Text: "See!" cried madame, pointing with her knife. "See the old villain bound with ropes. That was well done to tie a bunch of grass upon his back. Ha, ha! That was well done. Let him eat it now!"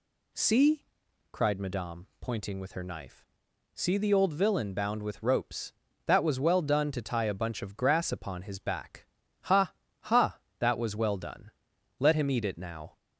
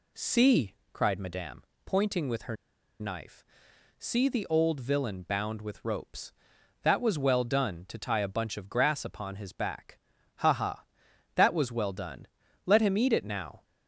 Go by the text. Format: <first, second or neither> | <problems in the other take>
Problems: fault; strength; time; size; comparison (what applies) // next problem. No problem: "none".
first | pauses between "her" and "knife"; at 2.5 s; 0.45 s long